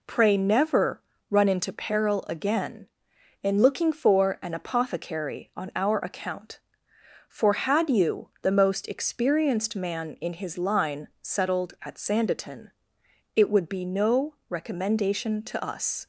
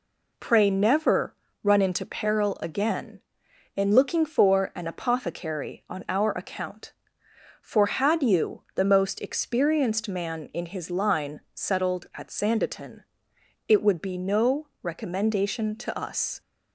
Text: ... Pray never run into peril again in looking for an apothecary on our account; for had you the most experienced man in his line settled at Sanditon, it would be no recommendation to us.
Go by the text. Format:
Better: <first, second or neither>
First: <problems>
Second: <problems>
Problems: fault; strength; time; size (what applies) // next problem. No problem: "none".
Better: neither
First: pauses between "never" and "run"; slight; at 0.9 s; 0.30 s long // pauses between "line" and "settled"; slight; at 11.0 s; 0.16 s long // pauses between "no" and "recommendation"; slight; at 14.3 s; 0.15 s long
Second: pauses between "never" and "run"; slight; at 1.3 s; 0.30 s long // pauses between "line" and "settled"; slight; at 11.3 s; 0.16 s long // pauses between "no" and "recommendation"; slight; at 14.6 s; 0.16 s long